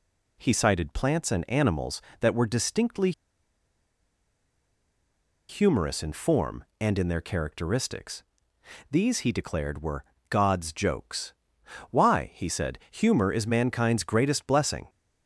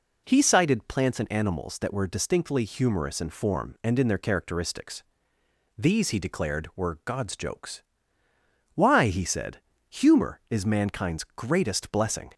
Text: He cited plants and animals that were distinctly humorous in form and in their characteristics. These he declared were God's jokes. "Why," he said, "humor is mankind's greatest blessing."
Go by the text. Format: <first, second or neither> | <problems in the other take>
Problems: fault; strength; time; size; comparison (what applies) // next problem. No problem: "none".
second | pauses between "distinctly" and "humorous"; strong; at 3.1 s; 2.3 s long // pauses between "were" and "God's"; slight; at 10.0 s; 0.26 s long